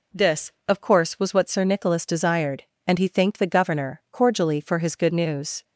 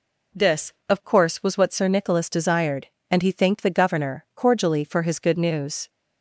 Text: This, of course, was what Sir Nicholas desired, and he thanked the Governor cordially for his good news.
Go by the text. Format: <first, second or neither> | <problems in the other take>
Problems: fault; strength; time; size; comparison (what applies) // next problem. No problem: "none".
neither | none